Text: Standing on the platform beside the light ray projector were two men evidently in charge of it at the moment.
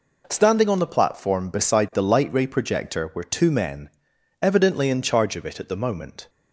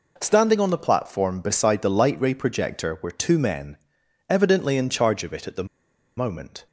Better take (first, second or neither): first